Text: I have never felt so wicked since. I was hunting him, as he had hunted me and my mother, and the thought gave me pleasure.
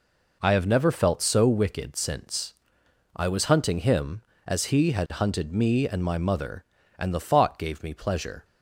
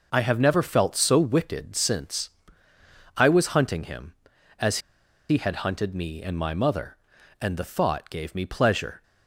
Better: first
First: none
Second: pauses between "as" and "he"; noticeable; at 4.7 s; 0.51 s long

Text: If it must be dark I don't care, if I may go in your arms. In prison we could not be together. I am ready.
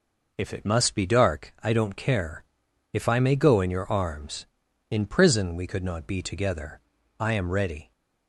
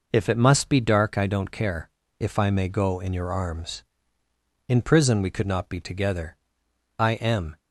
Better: first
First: none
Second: stops before "ready"; at 7.5 s

